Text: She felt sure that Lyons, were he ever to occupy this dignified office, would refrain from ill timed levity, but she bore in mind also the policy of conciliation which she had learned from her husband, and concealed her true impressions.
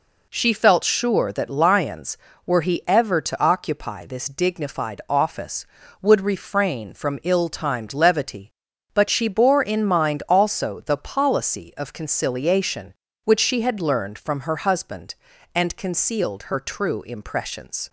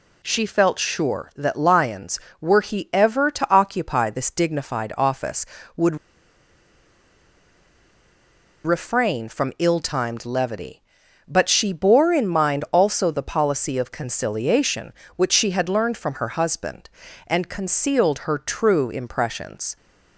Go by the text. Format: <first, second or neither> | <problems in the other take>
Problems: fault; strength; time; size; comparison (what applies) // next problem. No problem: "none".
first | pauses between "would" and "refrain"; strong; at 5.9 s; 2.6 s long